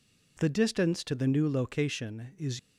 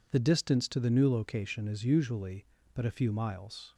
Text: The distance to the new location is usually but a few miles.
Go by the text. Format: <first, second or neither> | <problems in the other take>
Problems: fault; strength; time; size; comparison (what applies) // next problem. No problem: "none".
second | stops before "usually but a few miles"; at 2.5 s